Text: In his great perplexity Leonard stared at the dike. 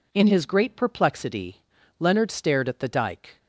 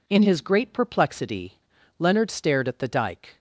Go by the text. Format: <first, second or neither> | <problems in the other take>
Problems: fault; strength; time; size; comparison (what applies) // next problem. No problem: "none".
neither | pauses between "perplexity" and "Leonard"; the same in both